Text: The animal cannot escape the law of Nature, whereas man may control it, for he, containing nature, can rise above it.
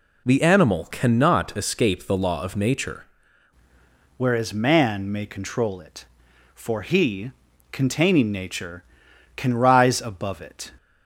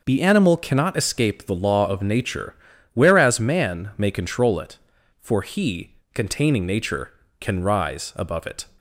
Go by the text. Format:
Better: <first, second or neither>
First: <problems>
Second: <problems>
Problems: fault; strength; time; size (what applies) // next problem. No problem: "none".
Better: second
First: changes voice at "whereas"; from 4.1 s on; 6.6 s long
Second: none